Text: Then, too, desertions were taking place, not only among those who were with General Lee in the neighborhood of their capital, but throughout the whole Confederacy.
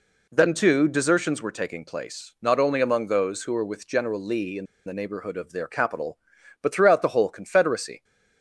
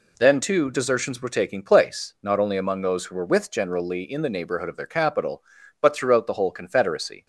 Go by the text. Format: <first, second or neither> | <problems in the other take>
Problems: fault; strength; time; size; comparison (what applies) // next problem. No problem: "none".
second | pauses between "in" and "the"; slight; at 4.6 s; 0.20 s long